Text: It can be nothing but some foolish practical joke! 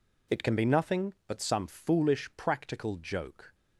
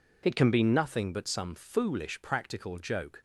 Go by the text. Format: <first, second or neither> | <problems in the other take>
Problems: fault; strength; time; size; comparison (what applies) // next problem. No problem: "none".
neither | none